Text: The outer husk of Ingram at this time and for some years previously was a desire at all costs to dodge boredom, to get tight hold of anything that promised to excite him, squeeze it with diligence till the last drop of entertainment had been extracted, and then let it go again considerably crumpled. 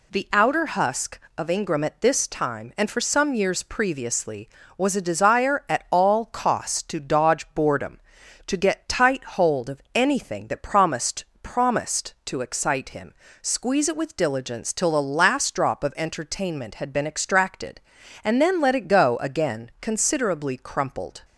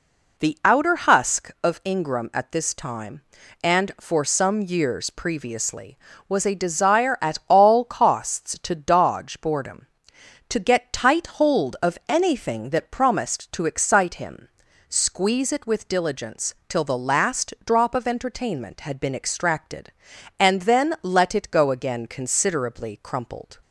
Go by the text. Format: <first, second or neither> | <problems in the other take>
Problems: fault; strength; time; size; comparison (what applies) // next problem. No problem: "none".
second | says "promised" twice; at 11.4 s